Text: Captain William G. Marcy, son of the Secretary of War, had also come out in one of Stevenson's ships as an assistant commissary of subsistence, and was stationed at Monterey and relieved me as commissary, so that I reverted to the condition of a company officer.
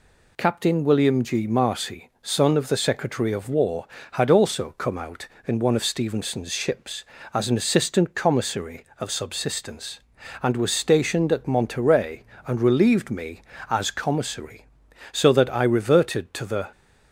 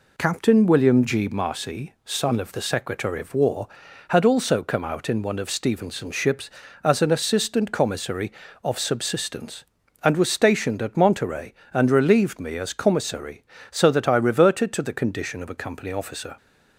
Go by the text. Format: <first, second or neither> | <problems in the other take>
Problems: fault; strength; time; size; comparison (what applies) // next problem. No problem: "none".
second | stops before "condition of a company officer"; at 16.7 s